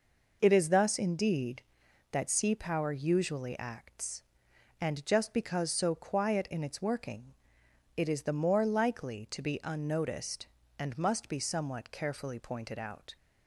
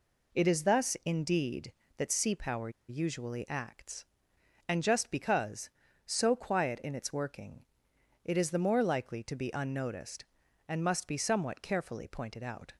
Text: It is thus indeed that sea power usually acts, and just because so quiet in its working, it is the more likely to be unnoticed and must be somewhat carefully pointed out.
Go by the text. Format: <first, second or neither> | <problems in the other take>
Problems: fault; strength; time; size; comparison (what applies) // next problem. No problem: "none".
first | pauses between "power" and "usually"; slight; at 2.6 s; 0.19 s long